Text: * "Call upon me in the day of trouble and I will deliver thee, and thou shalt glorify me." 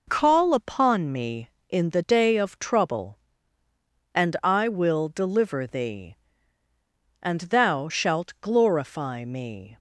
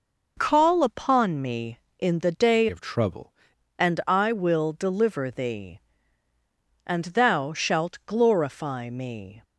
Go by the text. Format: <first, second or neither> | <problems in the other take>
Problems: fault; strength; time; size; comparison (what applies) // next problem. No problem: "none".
first | changes voice from "of" to "trouble"; from 2.6 to 3.3 s; 0.7 s long